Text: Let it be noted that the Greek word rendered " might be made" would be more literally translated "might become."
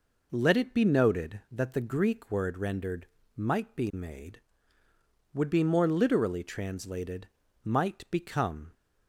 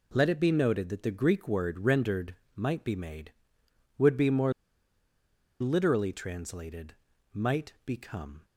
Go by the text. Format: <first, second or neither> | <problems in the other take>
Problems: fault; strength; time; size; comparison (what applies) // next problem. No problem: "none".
first | pauses between "more" and "literally"; at 4.5 s; 1.0 s long // pauses between "translated" and "might"; at 6.9 s; 0.40 s long; slight in the first